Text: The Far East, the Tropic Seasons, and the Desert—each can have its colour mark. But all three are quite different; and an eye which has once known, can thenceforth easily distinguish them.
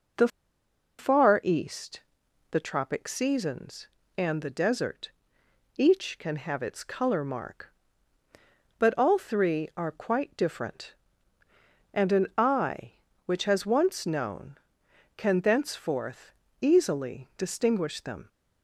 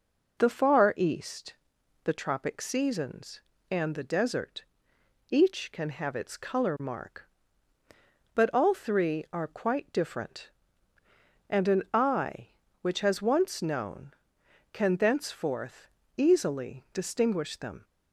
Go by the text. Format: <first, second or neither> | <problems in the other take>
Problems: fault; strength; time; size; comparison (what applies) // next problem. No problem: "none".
second | pauses between "The" and "Far"; noticeable; at 0.2 s; 0.71 s long // pauses between "thenceforth" and "easily"; slight; at 16.3 s; 0.26 s long; slight in the second